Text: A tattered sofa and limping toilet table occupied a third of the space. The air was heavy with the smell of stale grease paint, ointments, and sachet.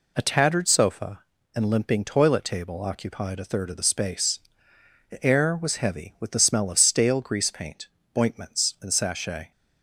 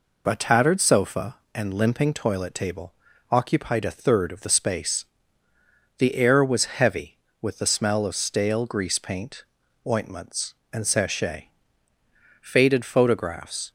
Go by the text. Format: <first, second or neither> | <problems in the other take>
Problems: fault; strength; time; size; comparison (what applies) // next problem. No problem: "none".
first | pauses between "table" and "occupied"; at 2.9 s; 0.38 s long // goes on to say "Faded photographs"; noticeable; from 12.4 s on; 1.2 s long